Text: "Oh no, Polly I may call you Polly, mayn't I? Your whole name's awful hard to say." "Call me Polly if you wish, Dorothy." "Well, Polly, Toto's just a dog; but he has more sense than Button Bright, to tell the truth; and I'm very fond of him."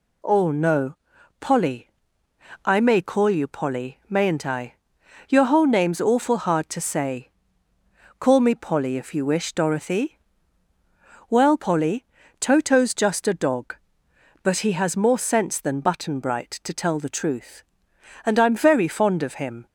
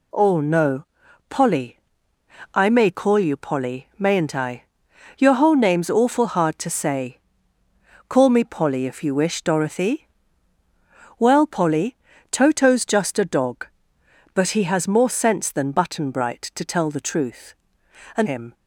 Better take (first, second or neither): first